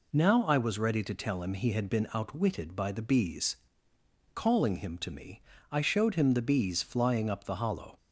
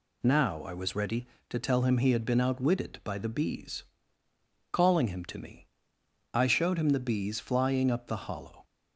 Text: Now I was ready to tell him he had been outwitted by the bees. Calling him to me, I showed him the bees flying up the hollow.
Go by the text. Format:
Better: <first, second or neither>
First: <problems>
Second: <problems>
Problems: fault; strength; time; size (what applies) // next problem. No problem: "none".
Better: neither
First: none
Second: none